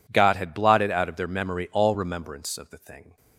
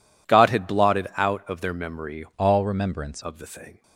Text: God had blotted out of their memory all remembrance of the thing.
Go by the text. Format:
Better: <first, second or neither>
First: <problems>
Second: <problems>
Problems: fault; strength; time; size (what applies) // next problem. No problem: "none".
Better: first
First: none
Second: changes voice from "all" to "remembrance"; from 2.3 to 3.2 s; 0.9 s long